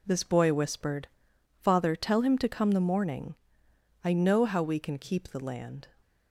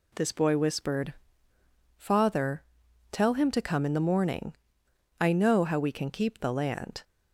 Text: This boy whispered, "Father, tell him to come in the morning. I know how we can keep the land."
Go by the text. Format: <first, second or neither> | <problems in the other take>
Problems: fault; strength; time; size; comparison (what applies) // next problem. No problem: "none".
second | skips "in"; at 2.7 s